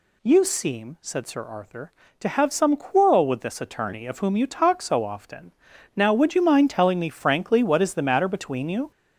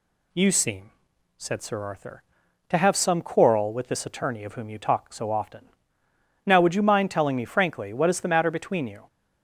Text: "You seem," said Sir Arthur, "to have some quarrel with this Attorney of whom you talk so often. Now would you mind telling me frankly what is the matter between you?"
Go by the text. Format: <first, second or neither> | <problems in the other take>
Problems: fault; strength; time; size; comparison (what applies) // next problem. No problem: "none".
second | gets louder; throughout; 6.5 dB